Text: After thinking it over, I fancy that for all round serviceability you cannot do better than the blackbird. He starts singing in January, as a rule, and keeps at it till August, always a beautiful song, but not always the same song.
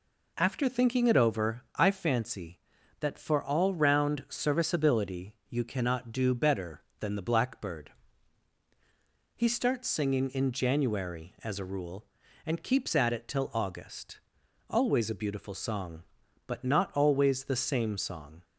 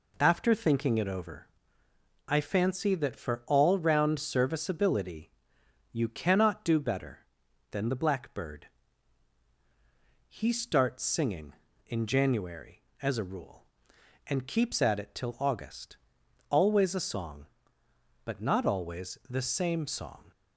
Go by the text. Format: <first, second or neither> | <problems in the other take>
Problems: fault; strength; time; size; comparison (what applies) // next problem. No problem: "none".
first | pauses between "serviceability" and "you"; noticeable; at 5.2 s; 0.62 s long // skips "beautiful"; at 16.9 s